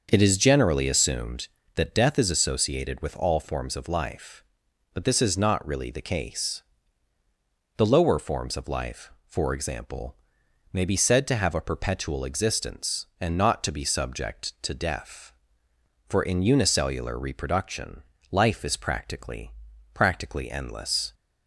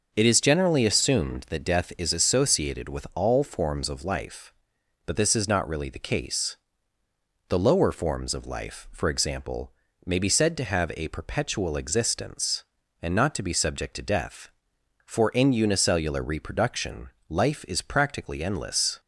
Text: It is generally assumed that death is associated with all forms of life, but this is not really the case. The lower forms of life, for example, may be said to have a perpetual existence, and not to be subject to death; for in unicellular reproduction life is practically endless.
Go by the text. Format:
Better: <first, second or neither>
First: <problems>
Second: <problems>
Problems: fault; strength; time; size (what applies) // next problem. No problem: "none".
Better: second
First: starts louder than the rest; until 1.1 s; 6.5 dB // pauses between "reproduction" and "life"; slight; at 18.0 s; 0.30 s long // says "practically" twice; at 19.9 s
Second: pauses between "reproduction" and "life"; slight; at 17.0 s; 0.22 s long